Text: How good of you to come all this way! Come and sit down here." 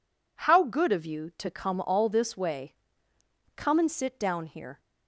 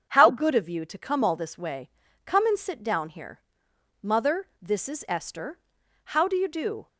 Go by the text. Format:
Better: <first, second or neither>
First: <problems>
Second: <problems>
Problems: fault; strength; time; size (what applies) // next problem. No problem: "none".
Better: first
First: none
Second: starts louder than the rest; until 1.1 s; 7 dB // goes on to say "Mother this is Esther How do you do"; strong; from 4.0 s on; 2.8 s long